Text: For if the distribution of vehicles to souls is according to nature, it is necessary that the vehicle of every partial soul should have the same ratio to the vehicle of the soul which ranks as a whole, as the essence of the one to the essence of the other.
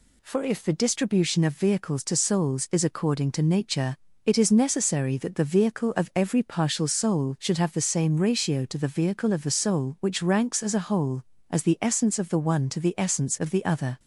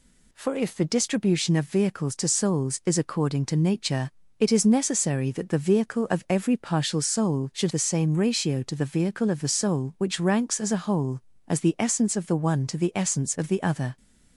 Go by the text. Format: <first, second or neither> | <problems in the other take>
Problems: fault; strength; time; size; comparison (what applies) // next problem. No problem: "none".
first | skips "have"; at 7.7 s